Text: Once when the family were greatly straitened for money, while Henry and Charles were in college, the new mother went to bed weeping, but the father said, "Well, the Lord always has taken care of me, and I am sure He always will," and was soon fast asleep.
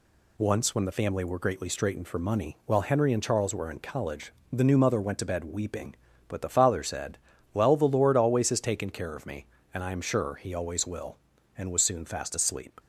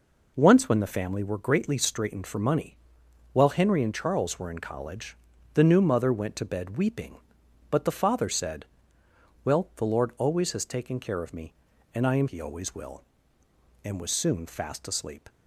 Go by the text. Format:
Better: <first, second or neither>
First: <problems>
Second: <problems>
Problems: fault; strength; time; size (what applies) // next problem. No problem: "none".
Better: first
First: none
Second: skips "sure"; at 12.2 s